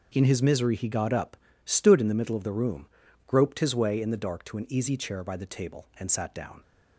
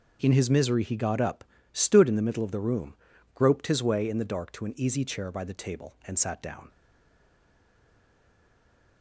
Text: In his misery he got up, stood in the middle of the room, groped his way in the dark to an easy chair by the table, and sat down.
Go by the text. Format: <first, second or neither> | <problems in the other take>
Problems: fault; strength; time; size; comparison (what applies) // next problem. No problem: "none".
first | stays silent after the last word; from 6.7 s on; 2.3 s long